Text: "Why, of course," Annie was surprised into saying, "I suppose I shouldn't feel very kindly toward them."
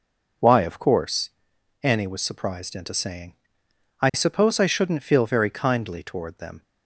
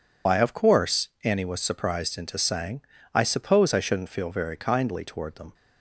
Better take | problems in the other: first | loses the start of "Why"; at 0.2 s; 115 ms

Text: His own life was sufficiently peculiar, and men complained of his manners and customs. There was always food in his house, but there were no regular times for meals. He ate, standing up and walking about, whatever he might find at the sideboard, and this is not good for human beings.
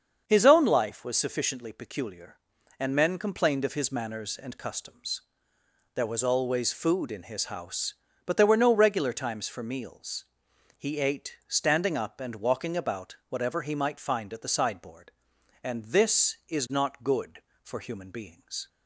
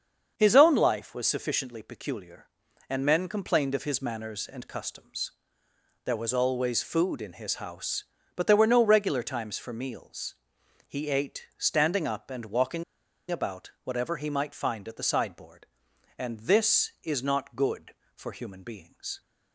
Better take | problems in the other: first | starts louder than the rest; until 1.3 s; 7 dB; also in the first // pauses between "walking" and "about"; noticeable; at 12.8 s; 0.46 s long

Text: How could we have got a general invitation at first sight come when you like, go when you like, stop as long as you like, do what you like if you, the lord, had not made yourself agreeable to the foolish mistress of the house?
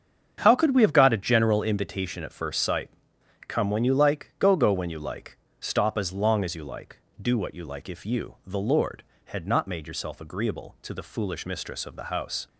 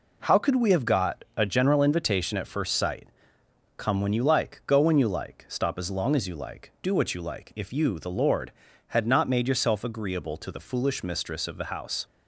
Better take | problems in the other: second | starts louder than the rest; strong; until 1.4 s; 8 dB // pauses between "sight" and "come"; noticeable; at 2.8 s; 0.60 s long; noticeable in the second // says "go" twice; at 4.5 s

